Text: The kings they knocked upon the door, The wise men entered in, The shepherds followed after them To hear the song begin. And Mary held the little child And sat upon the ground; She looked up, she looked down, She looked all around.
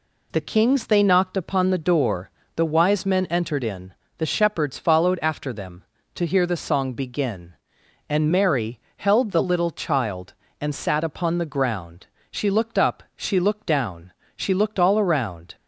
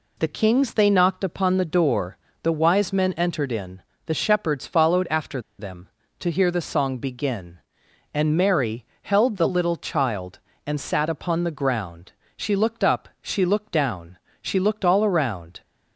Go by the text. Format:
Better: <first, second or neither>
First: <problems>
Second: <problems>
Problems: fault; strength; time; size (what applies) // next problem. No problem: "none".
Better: first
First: pauses between "Mary" and "held"; slight; at 8.7 s; 0.18 s long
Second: pauses between "after" and "them"; slight; at 5.4 s; 0.18 s long // pauses between "Mary" and "held"; slight; at 8.8 s; 0.18 s long